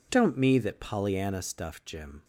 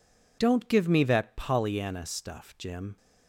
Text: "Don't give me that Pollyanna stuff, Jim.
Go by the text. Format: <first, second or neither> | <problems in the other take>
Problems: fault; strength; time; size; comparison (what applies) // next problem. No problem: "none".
second | skips "give"; at 0.3 s